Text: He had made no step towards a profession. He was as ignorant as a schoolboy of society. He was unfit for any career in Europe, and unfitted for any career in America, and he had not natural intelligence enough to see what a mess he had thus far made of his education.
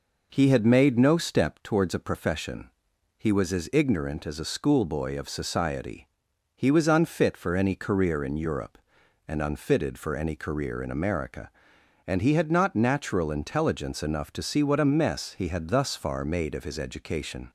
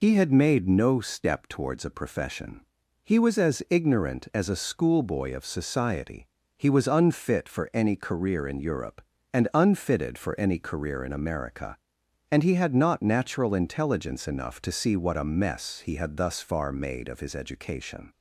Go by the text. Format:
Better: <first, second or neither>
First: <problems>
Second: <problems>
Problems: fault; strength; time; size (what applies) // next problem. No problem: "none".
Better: first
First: none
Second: loses the start of "He"; at 0.0 s; 45 ms